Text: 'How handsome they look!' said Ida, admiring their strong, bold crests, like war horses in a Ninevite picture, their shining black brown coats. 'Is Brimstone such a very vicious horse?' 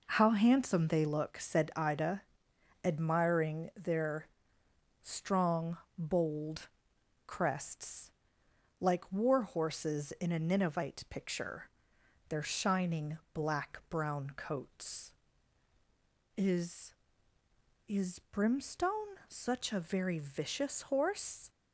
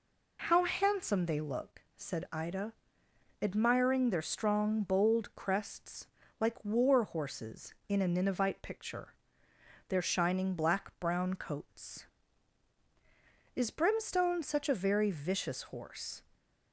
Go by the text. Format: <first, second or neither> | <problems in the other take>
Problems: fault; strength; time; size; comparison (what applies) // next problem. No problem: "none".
second | pauses between "their" and "strong"; noticeable; at 4.2 s; 0.74 s long // pauses between "bold" and "crests"; noticeable; at 6.6 s; 0.58 s long // says "Is" twice; at 17.8 s